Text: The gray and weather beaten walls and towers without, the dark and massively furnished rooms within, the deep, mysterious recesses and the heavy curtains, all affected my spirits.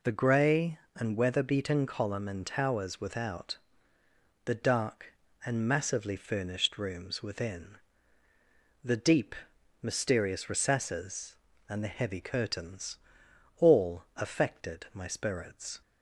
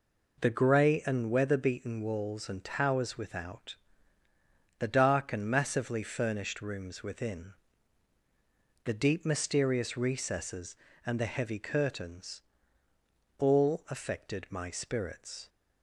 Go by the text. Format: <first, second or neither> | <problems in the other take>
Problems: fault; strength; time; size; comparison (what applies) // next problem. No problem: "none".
second | says "column" for "walls"; at 1.8 s